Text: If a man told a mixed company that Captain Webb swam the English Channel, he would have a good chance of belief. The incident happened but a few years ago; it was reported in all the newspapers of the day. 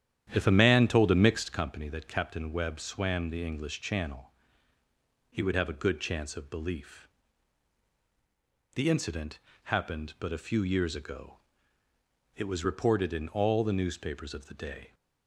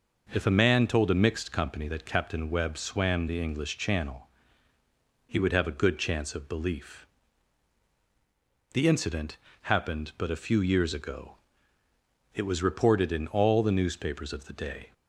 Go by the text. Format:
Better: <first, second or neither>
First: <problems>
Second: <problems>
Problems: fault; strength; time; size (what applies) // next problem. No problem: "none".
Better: second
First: starts louder than the rest; strong; until 1.6 s; 10.5 dB // pauses between "incident" and "happened"; slight; at 9.3 s; 0.26 s long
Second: pauses between "incident" and "happened"; slight; at 9.3 s; 0.26 s long